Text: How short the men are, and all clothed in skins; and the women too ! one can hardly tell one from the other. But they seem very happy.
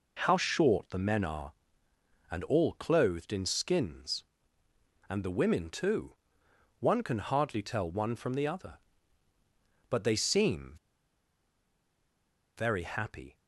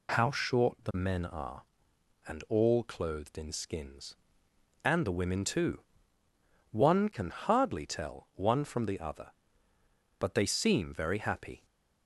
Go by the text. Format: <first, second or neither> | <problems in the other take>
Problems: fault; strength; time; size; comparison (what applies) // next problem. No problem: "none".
second | pauses between "seem" and "very"; strong; at 10.7 s; 1.8 s long